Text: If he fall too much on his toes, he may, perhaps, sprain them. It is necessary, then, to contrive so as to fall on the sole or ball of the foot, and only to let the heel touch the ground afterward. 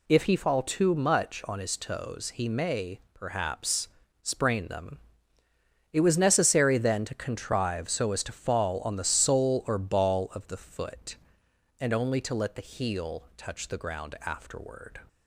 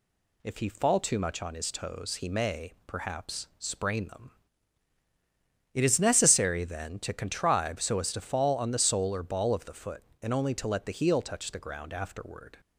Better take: second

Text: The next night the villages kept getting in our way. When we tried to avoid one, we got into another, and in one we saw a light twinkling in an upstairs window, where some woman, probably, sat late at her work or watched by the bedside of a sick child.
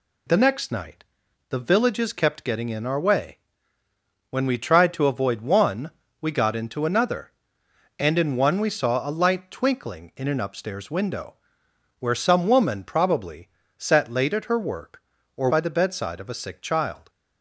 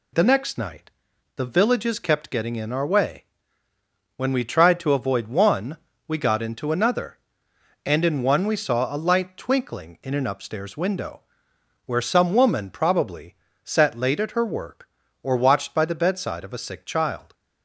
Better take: second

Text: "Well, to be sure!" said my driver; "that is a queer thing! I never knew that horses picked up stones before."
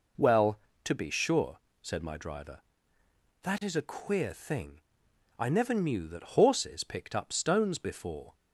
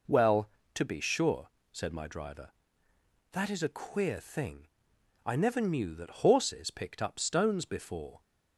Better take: neither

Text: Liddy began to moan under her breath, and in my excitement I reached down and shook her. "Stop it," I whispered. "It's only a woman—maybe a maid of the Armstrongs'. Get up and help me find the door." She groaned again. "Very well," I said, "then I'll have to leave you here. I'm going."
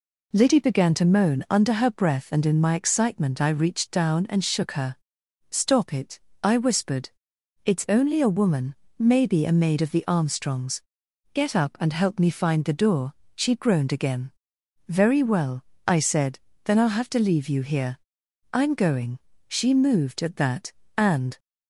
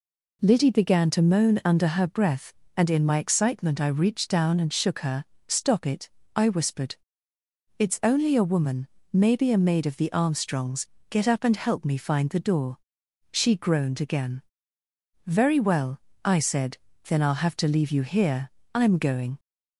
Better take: second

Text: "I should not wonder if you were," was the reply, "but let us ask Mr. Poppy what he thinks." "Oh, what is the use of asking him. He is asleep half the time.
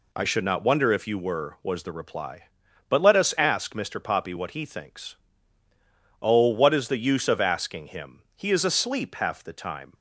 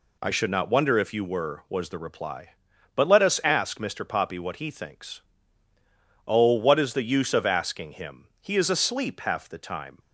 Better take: neither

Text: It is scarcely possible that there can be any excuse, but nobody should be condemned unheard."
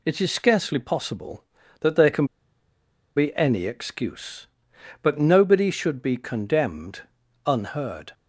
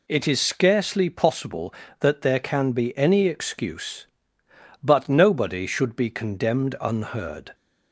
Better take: second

